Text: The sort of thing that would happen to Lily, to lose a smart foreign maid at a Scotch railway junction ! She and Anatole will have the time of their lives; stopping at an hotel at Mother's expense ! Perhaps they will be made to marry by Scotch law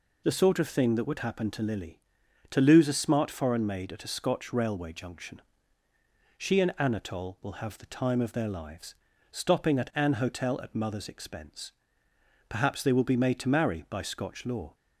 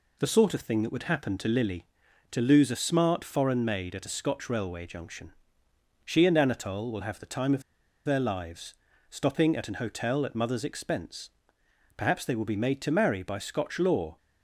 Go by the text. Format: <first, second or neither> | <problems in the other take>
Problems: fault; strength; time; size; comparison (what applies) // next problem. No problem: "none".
first | pauses between "of" and "their"; at 7.6 s; 0.44 s long